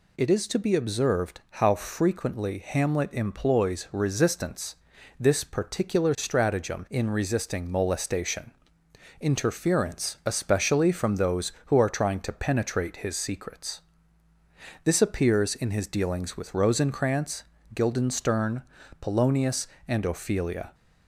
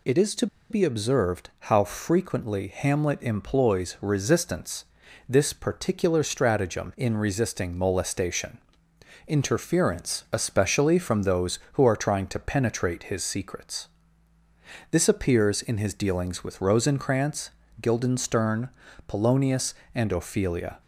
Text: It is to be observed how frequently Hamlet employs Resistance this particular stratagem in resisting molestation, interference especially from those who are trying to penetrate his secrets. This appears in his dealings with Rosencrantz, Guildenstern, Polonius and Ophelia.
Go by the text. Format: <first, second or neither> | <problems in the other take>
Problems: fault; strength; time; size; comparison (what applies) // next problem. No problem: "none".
first | pauses between "to" and "be"; slight; at 0.4 s; 0.24 s long // pauses between "Resistance" and "this"; at 4.8 s; 0.42 s long; also in the first